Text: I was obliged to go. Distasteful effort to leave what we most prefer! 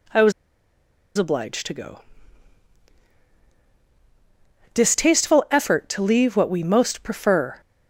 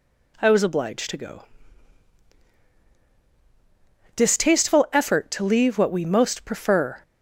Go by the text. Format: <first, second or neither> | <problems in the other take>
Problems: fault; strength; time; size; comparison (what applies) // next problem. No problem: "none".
second | pauses between "was" and "obliged"; noticeable; at 0.3 s; 0.85 s long